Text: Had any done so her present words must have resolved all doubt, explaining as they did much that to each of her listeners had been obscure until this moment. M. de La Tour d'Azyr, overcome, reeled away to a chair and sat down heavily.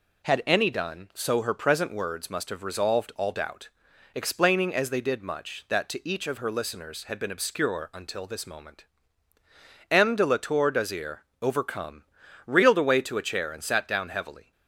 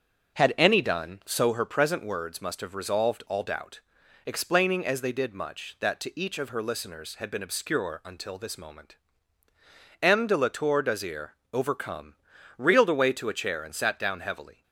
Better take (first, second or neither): first